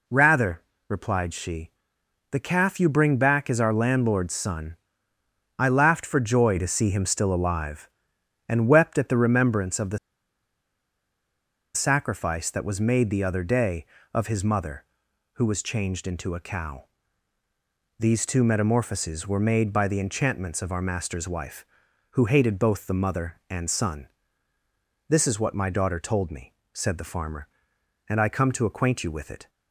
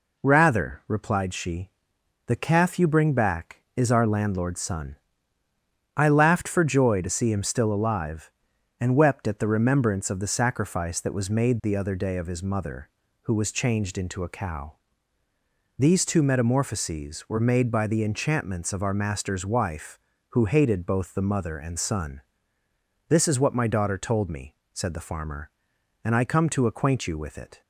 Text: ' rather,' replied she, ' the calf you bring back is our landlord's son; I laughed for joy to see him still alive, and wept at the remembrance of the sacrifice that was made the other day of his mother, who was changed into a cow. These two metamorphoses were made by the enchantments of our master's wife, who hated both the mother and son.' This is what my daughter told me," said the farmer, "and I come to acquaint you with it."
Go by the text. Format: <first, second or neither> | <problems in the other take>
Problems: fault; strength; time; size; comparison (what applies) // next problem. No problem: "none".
second | pauses between "the" and "sacrifice"; strong; at 9.9 s; 1.7 s long